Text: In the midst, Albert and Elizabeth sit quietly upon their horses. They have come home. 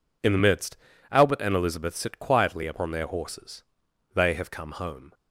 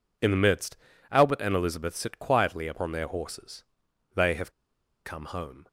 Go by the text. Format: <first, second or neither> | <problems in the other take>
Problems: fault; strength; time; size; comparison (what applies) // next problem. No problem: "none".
first | pauses between "have" and "come"; noticeable; at 4.5 s; 0.54 s long